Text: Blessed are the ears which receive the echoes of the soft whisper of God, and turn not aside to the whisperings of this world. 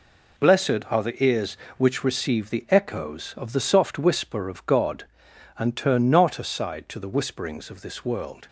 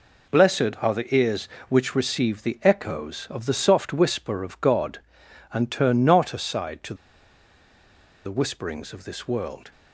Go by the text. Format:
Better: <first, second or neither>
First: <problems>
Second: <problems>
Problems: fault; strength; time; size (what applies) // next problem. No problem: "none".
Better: first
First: none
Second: pauses between "to" and "the"; strong; at 6.9 s; 1.3 s long